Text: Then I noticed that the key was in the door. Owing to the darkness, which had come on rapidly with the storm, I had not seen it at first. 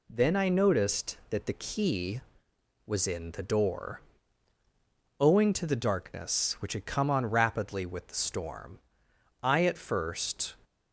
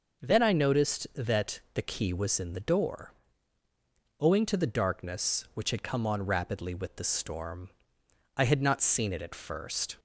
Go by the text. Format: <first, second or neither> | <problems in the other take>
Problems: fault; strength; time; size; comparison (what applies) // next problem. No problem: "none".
second | skips "had not seen it"; at 9.6 s